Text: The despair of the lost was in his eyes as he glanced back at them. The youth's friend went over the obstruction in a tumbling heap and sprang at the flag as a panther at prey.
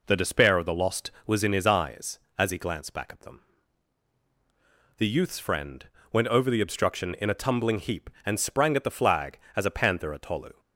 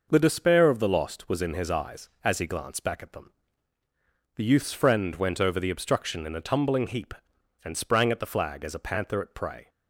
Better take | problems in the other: second | pauses between "friend" and "went"; slight; at 5.8 s; 0.26 s long // says "tolu" for "prey"; at 10.2 s

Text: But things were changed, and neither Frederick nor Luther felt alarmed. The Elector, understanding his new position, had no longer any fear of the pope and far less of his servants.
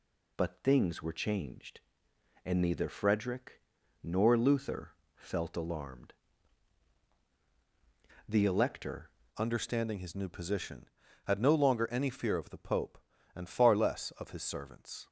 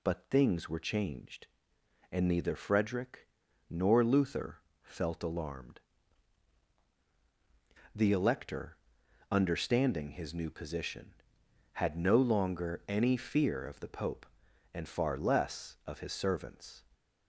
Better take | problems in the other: second | pauses between "Frederick" and "nor"; at 3.6 s; 0.42 s long; also in the second // pauses between "Luther" and "felt"; slight; at 4.9 s; 0.20 s long; slight in the second // changes voice at "understanding"; from 9.3 s on; 5.7 s long

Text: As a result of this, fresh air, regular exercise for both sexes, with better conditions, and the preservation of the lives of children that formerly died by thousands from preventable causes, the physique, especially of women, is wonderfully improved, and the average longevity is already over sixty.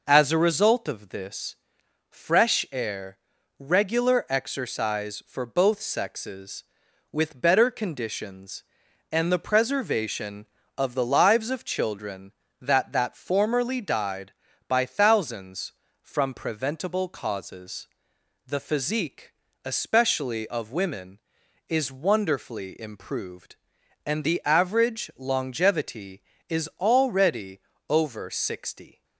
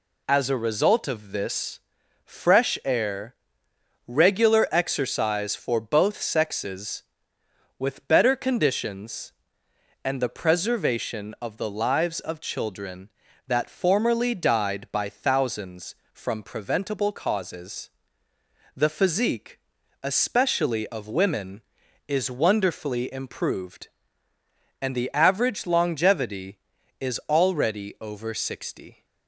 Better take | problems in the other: second | says "that" twice; at 12.9 s // pauses between "already" and "over"; slight; at 27.6 s; 0.28 s long

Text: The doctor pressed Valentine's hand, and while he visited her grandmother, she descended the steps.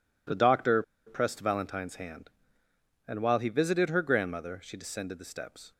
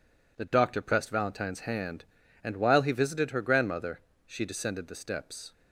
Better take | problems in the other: second | pauses between "doctor" and "pressed"; slight; at 0.8 s; 0.24 s long

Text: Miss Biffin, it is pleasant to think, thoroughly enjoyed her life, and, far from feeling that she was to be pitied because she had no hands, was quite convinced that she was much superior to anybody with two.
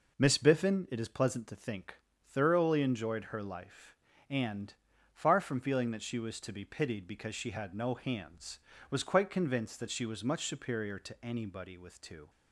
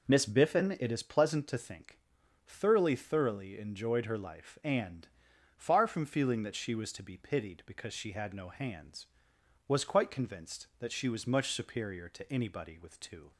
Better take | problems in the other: first | says "thoroughly" twice; at 2.9 s

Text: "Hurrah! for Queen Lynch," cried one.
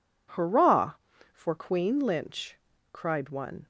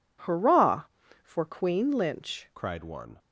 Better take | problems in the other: first | changes voice at "cried"; from 2.5 s on; 0.6 s long

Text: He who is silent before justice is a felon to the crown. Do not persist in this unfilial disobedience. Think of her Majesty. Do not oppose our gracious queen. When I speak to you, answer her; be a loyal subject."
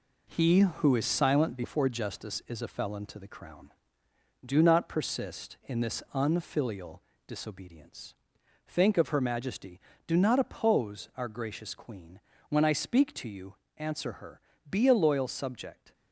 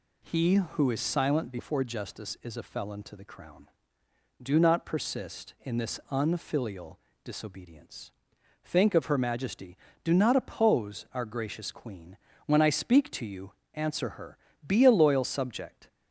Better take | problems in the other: second | gets quieter; noticeable; throughout; 5 dB // pauses between "unfilial" and "disobedience"; slight; at 7.0 s; 0.28 s long; slight in the second

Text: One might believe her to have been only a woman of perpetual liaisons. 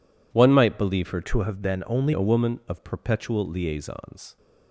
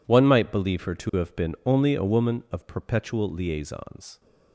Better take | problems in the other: second | changes voice from "to" to "only"; from 1.2 to 2.1 s; 0.9 s long

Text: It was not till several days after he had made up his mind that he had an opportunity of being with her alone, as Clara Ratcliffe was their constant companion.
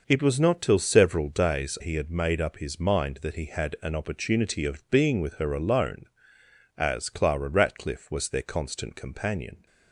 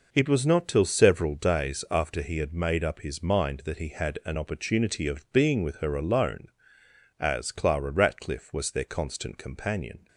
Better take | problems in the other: second | skips "after"; at 1.7 s

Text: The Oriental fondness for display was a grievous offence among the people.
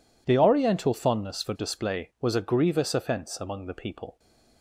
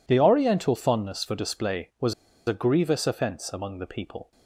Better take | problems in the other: first | pauses between "was" and "a"; slight; at 2.1 s; 0.35 s long

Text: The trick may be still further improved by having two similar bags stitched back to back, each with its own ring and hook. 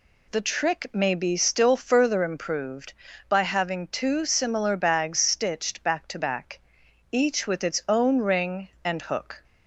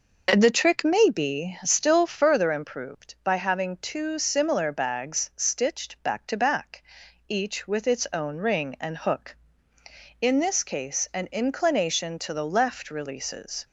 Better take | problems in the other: first | goes on to say "In this case an inclination to the left releases"; strong; from 10.2 s on; 3.4 s long

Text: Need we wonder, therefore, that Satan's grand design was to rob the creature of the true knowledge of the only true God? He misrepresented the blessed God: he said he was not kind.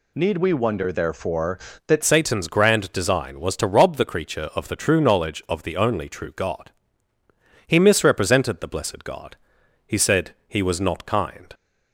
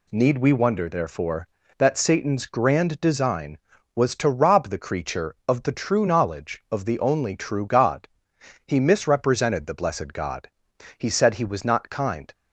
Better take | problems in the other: second | changes voice at "Satan's"; from 2.0 s on; 9.5 s long // pauses between "said" and "he"; slight; at 10.3 s; 0.16 s long

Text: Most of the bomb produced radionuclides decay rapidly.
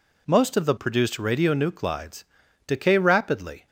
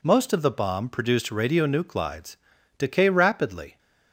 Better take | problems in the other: second | skips "bomb"; at 0.7 s // pauses between "radionuclides" and "decay"; at 2.2 s; 0.42 s long; also in the second

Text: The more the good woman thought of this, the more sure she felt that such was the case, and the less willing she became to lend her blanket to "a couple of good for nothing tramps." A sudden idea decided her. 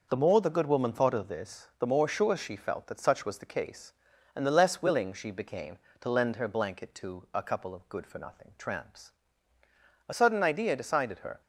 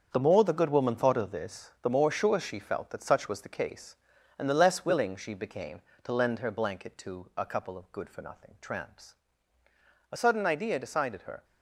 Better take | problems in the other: first | gets quieter; strong; throughout; 9.5 dB

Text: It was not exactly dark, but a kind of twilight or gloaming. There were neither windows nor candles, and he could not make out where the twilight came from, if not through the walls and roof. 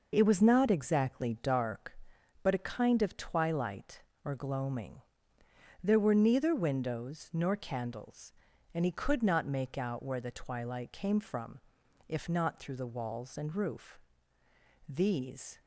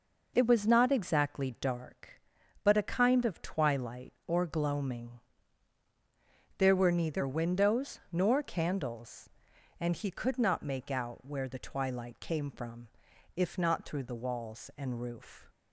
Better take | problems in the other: second | goes on to say "These"; noticeable; from 14.8 s on; 0.74 s long

